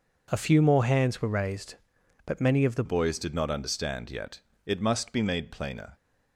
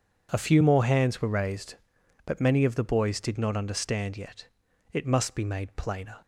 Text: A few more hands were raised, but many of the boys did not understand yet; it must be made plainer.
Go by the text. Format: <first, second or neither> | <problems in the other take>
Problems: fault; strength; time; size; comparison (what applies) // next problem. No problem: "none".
second | changes voice at "boys"; from 2.8 s on; 3.1 s long